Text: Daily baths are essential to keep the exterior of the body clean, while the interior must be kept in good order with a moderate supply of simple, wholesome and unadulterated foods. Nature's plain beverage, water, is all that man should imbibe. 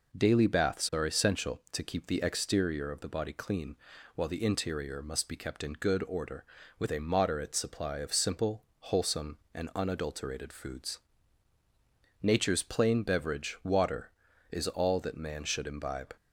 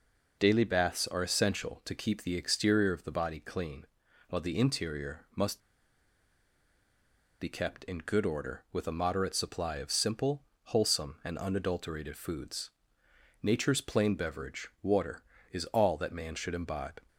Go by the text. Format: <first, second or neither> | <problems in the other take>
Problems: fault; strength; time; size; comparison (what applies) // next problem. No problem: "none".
first | pauses between "must" and "be"; strong; at 5.5 s; 1.8 s long